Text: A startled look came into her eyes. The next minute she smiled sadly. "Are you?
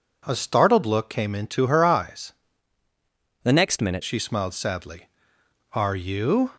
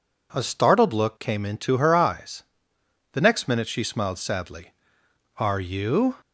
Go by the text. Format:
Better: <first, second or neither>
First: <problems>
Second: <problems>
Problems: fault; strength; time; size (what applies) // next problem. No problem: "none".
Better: second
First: changes voice from "The" to "minute"; from 3.4 to 4.0 s; 0.6 s long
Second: none